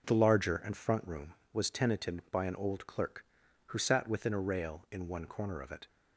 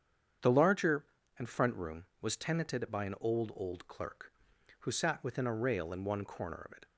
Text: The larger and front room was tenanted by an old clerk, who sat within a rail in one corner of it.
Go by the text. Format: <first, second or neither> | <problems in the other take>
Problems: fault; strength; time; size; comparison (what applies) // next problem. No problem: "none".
first | starts louder than the rest; strong; until 1.7 s; 8 dB // says "old" twice; at 3.5 s